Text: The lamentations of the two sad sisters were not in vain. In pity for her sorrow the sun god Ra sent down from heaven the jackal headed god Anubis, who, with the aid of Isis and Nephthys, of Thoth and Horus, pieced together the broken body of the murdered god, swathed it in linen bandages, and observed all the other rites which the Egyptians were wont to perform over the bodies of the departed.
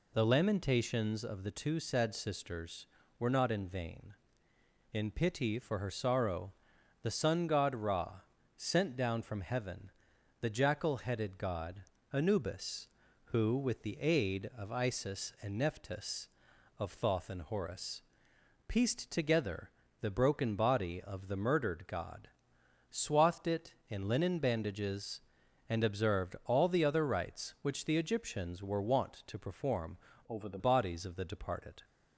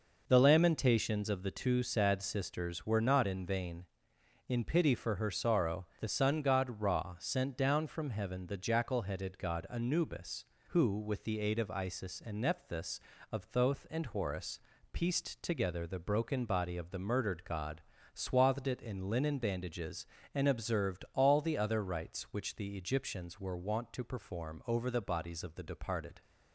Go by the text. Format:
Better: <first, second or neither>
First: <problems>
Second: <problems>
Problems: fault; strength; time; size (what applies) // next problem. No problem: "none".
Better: second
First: pauses between "sorrow" and "the"; noticeable; at 6.5 s; 0.50 s long // pauses between "Ra" and "sent"; slight; at 8.1 s; 0.36 s long // pauses between "heaven" and "the"; noticeable; at 9.8 s; 0.50 s long // pauses between "god" and "Anubis"; slight; at 11.8 s; 0.30 s long // pauses between "together" and "the"; slight; at 19.7 s; 0.28 s long // changes voice from "over" to "the"; from 30.2 to 30.5 s; 0.3 s long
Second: pauses between "sorrow" and "the"; slight; at 5.8 s; 0.16 s long